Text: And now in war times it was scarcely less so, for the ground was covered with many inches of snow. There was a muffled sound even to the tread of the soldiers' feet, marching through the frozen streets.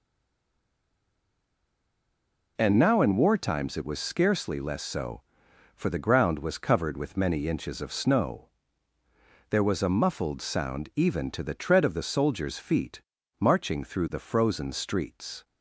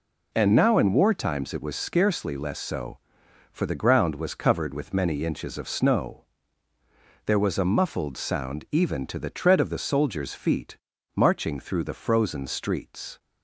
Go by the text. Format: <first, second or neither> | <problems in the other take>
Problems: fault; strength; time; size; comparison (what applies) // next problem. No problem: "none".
second | stays silent before the first word; strong; until 2.5 s; 2.5 s long